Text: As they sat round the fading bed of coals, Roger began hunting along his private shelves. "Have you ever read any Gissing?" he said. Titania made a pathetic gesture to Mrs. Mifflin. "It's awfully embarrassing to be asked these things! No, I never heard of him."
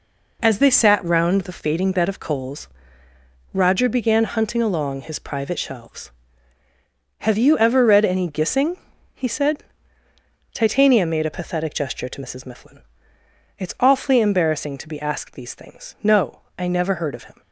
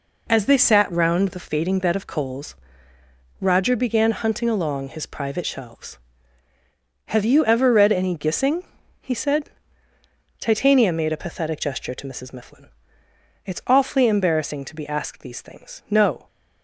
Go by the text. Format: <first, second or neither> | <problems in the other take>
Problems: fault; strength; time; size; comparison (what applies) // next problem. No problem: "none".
first | stops before "I never heard of him"; at 16.2 s